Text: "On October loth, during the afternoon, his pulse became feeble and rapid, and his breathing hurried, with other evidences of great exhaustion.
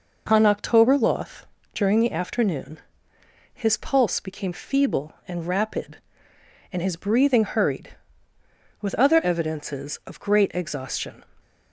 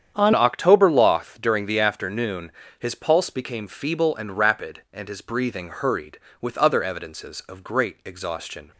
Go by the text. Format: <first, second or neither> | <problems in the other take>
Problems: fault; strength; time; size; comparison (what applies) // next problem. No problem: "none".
first | starts louder than the rest; strong; until 1.1 s; 8.5 dB // changes voice at "October"; from 0.3 s on; 8.4 s long